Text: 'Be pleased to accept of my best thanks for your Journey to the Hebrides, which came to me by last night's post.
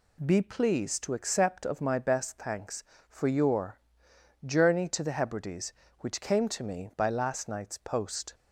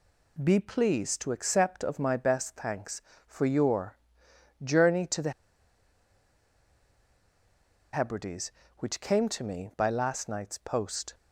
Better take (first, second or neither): first